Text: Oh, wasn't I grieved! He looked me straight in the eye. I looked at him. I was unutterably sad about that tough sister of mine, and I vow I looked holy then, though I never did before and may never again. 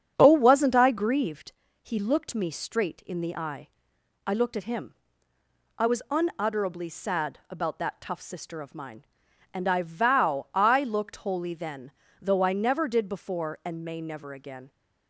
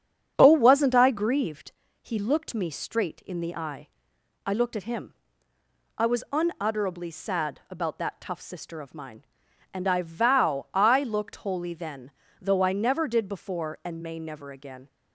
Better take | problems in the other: neither | starts louder than the rest; strong; the same in both

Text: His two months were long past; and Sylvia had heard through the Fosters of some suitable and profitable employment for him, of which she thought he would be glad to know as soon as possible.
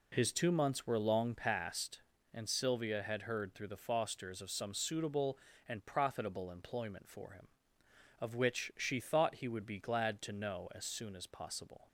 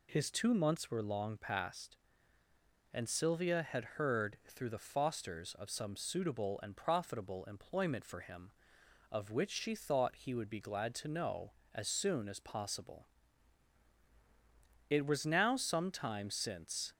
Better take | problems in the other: first | goes on to say "It was now some time since"; strong; from 14.8 s on; 2.0 s long

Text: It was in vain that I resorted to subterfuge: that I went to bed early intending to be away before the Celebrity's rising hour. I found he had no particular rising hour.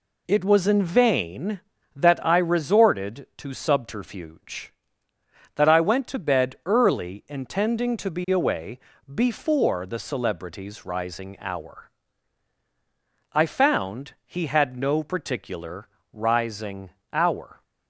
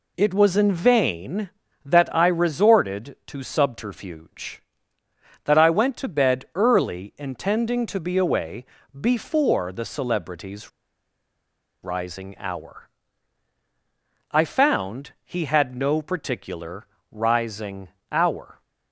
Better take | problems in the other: first | pauses between "away" and "before"; slight; at 8.6 s; 0.28 s long; slight in the first // pauses between "Celebrity's" and "rising"; at 10.7 s; 1.1 s long // pauses between "particular" and "rising"; slight; at 16.8 s; 0.24 s long; slight in the first // pauses between "rising" and "hour"; slight; at 17.8 s; 0.20 s long; slight in the first

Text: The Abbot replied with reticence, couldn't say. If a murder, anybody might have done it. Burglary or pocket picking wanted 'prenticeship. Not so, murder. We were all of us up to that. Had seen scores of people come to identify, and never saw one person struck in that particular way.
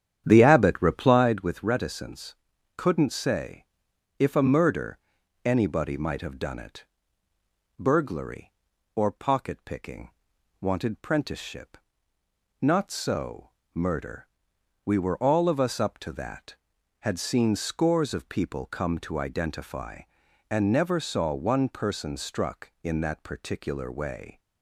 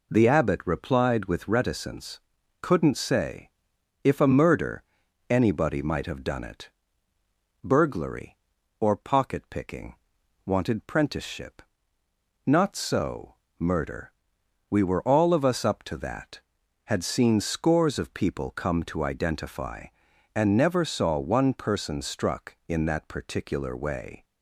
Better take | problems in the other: second | starts louder than the rest; strong; until 1.4 s; 9.5 dB // pauses between "picking" and "wanted"; noticeable; at 10.0 s; 0.52 s long; noticeable in the second

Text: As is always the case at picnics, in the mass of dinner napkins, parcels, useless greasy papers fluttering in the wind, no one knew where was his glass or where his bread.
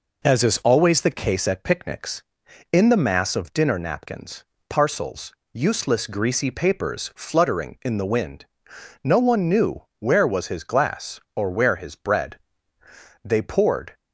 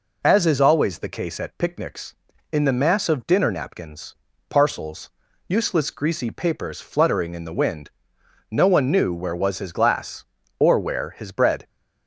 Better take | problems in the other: second | goes on to say "They poured"; noticeable; from 13.2 s on; 0.72 s long

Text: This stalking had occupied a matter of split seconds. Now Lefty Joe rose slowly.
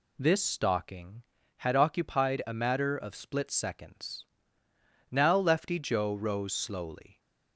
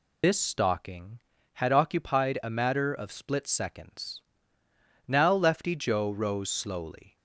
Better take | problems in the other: first | loses the start of "This"; at 0.2 s; 95 ms

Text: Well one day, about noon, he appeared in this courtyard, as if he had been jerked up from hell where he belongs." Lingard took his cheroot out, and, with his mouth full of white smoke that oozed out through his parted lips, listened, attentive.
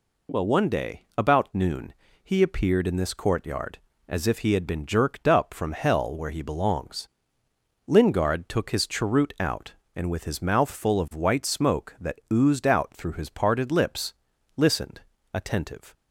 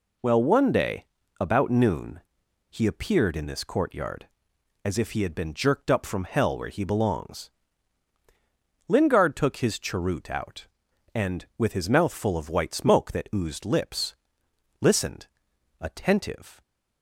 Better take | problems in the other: first | skips "out through his parted"; at 13.6 s

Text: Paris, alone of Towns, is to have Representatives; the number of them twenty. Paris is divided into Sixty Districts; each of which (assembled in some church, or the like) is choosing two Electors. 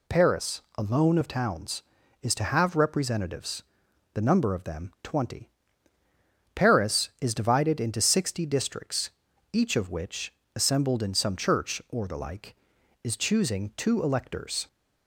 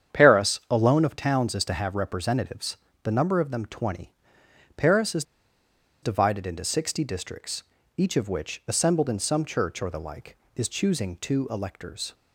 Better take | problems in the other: first | starts louder than the rest; strong; until 1.2 s; 8.5 dB // pauses between "is" and "divided"; noticeable; at 5.2 s; 0.80 s long

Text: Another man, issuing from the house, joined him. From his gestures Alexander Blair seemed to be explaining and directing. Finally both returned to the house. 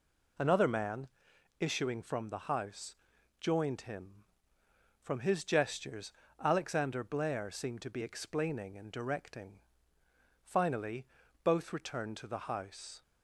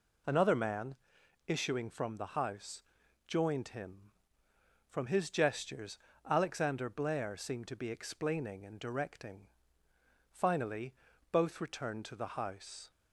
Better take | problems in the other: neither | pauses between "gestures" and "Alexander"; slight; the same in both // pauses between "Finally" and "both"; slight; the same in both

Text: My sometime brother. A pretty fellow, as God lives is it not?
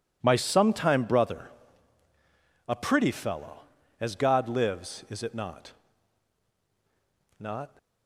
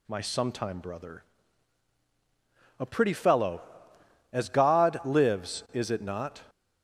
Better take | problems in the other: second | says "not" twice; at 7.3 s

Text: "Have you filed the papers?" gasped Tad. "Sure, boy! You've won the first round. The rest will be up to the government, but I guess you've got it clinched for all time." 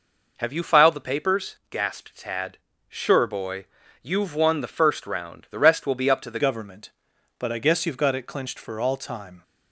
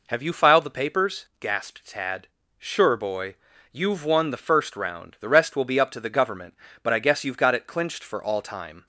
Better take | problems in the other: second | changes voice at "government"; from 6.3 s on; 3.1 s long

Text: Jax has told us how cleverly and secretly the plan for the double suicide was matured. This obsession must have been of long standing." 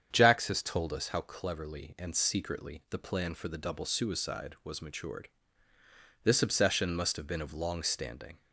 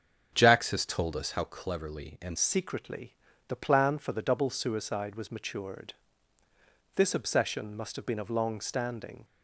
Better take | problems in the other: first | starts louder than the rest; strong; until 1.3 s; 7.5 dB; strong in the first // changes voice at "secretly"; from 2.3 s on; 6.9 s long // pauses between "secretly" and "the"; at 3.1 s; 0.38 s long

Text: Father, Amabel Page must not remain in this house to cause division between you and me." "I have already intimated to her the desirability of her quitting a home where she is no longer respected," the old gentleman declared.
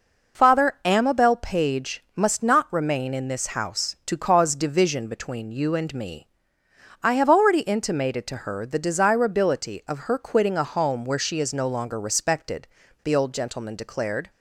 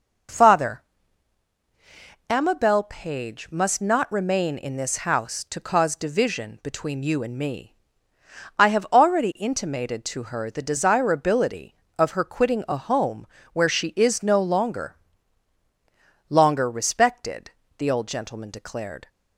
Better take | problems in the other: first | pauses between "home" and "where"; slight; at 13.2 s; 0.26 s long // says "longer" twice; at 16.3 s

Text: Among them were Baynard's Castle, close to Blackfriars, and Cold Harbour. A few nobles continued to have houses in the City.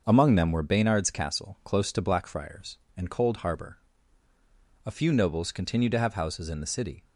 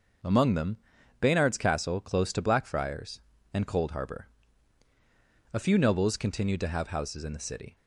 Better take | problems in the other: first | starts louder than the rest; noticeable; until 1.6 s; 6 dB; also in the first // skips "were"; at 0.9 s

